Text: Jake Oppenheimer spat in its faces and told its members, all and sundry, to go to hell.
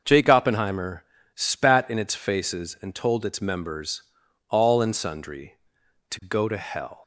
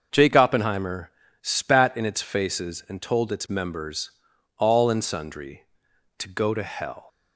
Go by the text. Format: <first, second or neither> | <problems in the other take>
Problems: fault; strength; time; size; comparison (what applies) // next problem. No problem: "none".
neither | starts louder than the rest; the same in both // pauses between "Oppenheimer" and "spat"; slight; the same in both